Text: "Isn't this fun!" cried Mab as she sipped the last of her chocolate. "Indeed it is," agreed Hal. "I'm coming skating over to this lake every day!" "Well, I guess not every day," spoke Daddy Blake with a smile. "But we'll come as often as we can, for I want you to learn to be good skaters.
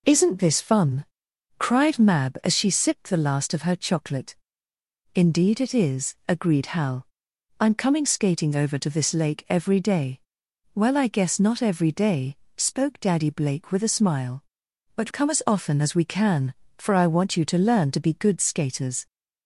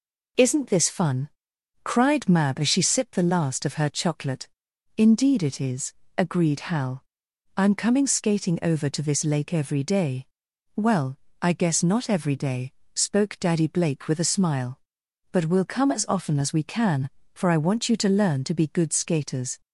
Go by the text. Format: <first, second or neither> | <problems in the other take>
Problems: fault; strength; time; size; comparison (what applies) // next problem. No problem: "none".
second | skips "we'll"; at 15.0 s